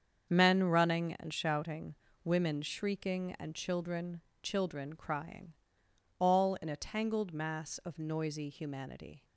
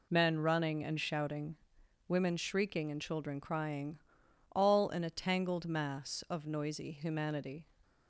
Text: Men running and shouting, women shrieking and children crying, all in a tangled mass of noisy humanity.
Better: second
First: starts louder than the rest; strong; until 1.3 s; 7 dB // says "children" twice; at 4.4 s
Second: none

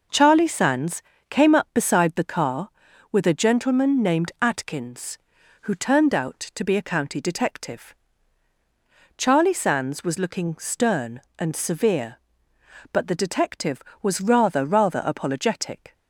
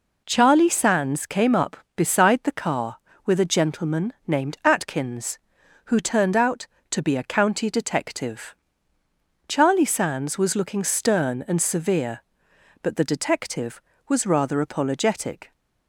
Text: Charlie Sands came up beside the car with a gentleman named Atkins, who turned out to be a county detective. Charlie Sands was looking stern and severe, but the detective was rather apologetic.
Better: second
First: pauses between "Sands" and "came"; slight; at 1.0 s; 0.26 s long // says "rather" twice; at 14.6 s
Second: none

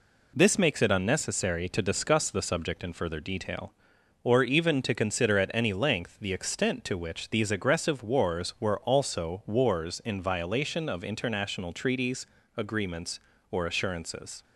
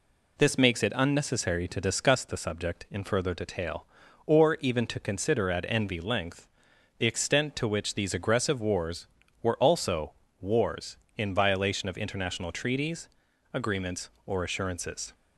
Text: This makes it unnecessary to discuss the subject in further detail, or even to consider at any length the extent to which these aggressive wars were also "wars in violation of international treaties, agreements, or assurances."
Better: first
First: none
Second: says "envy" for "any"; at 5.6 s // pauses between "length" and "the"; noticeable; at 6.4 s; 0.52 s long // pauses between "also" and "wars"; slight; at 10.1 s; 0.28 s long

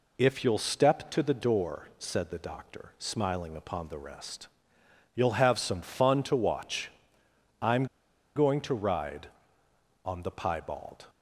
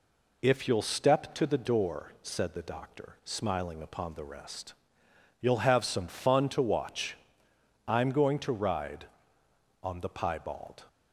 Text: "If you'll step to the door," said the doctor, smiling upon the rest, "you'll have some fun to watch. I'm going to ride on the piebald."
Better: second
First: pauses between "I'm" and "going"; noticeable; at 7.8 s; 0.50 s long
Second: none

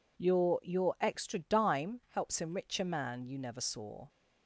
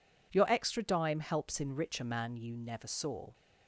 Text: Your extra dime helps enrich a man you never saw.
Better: second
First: says "Your" twice; at 0.6 s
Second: none

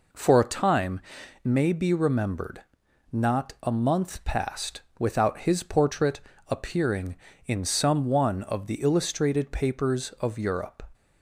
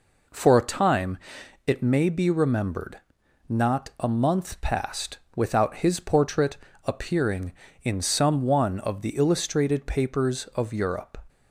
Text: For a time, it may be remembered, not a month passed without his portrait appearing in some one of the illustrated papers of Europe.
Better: second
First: skips "it"; at 1.2 s // pauses between "passed" and "without"; slight; at 4.8 s; 0.18 s long // pauses between "portrait" and "appearing"; slight; at 6.1 s; 0.28 s long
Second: pauses between "passed" and "without"; slight; at 5.1 s; 0.18 s long // pauses between "portrait" and "appearing"; slight; at 6.5 s; 0.28 s long

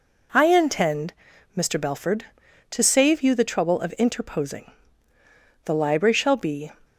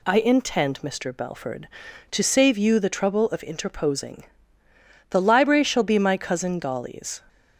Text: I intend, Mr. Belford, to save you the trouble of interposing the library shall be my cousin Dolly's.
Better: second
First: pauses between "interposing" and "the"; noticeable; at 4.7 s; 0.94 s long // stops before "my cousin Dolly's"; at 6.8 s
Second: pauses between "interposing" and "the"; noticeable; at 4.2 s; 0.86 s long

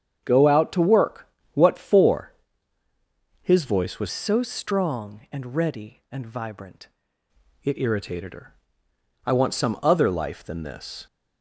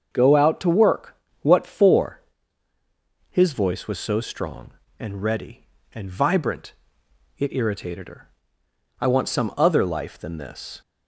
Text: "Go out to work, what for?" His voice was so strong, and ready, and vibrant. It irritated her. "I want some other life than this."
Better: second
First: starts louder than the rest; strong; until 1.2 s; 7.5 dB // changes voice from "so" to "vibrant"; from 4.1 to 6.8 s; 2.7 s long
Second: starts louder than the rest; until 1.1 s; 6.5 dB

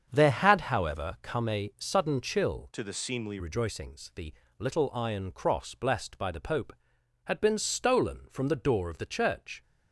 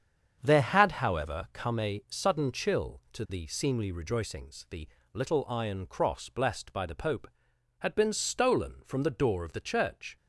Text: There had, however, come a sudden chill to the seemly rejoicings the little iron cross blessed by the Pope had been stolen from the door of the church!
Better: second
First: starts louder than the rest; strong; until 1.1 s; 7.5 dB // changes voice from "to" to "seemly"; from 2.7 to 3.3 s; 0.6 s long // pauses between "the" and "little"; slight; at 4.3 s; 0.26 s long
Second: starts louder than the rest; strong; until 1.4 s; 7.5 dB // pauses between "the" and "little"; slight; at 4.8 s; 0.26 s long

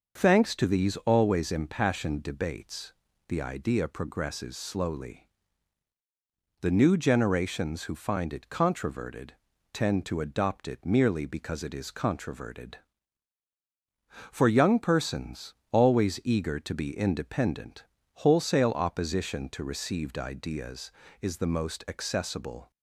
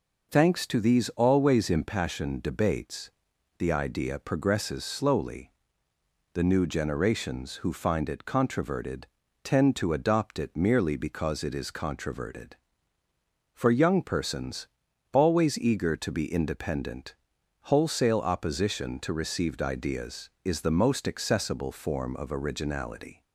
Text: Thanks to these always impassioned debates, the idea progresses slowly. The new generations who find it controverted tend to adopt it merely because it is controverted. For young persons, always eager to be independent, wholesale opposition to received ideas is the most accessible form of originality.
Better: second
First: starts louder than the rest; until 1.2 s; 6.5 dB // pauses between "controverted" and "tend"; at 9.3 s; 0.40 s long // stops before "form of originality"; at 22.7 s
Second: pauses between "controverted" and "tend"; slight; at 9.0 s; 0.36 s long

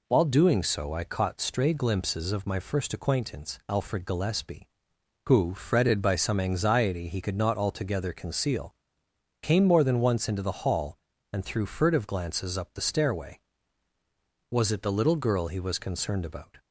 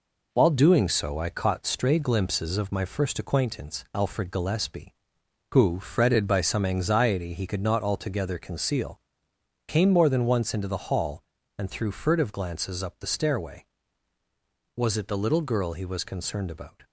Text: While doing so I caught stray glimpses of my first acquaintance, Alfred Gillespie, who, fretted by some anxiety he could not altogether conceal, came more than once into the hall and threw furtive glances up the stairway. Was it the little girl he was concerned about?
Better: first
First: none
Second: gets quieter; noticeable; throughout; 5.5 dB

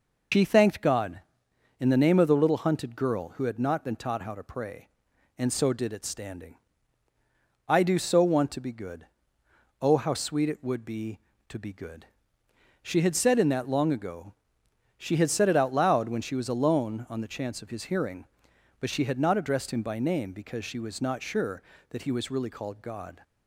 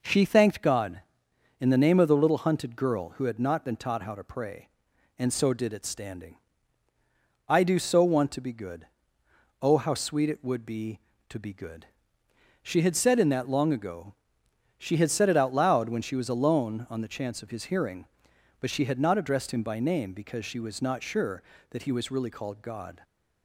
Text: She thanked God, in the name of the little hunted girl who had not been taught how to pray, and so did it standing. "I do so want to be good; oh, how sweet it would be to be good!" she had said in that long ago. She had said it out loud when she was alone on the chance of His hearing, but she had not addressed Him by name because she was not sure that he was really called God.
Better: second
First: loses the start of "She"; at 0.3 s; 110 ms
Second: none

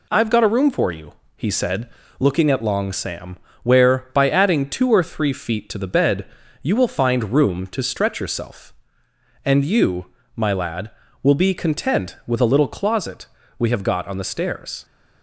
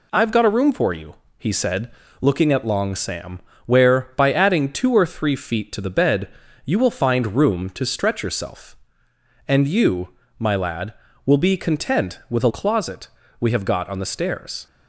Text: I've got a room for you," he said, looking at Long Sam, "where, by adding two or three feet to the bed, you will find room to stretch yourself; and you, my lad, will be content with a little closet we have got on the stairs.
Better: first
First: pauses between "closet" and "we"; slight; at 13.2 s; 0.32 s long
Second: skips "little"; at 12.5 s // pauses between "closet" and "we"; slight; at 13.0 s; 0.32 s long

